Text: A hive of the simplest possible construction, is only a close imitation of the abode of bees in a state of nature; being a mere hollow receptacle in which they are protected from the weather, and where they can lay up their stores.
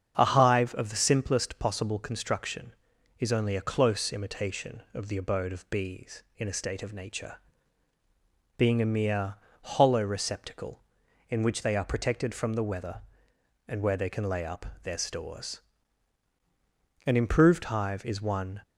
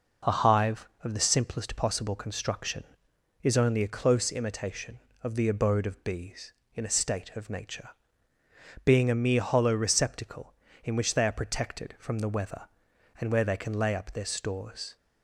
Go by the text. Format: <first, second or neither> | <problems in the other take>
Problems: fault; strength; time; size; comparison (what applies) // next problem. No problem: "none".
second | starts louder than the rest; strong; until 1.2 s; 7.5 dB // pauses between "mere" and "hollow"; slight; at 9.3 s; 0.28 s long // pauses between "up" and "their"; slight; at 14.6 s; 0.20 s long // goes on to say "An improved hive is one"; from 17.0 s on; 1.5 s long